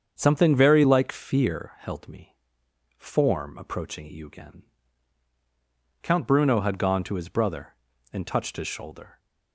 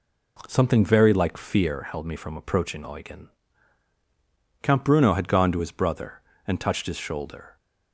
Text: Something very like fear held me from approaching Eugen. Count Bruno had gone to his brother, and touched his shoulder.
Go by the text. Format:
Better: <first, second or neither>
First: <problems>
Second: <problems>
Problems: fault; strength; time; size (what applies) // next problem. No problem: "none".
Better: second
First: starts louder than the rest; strong; until 1.2 s; 7 dB // says "form" for "from"; at 2.9 s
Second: none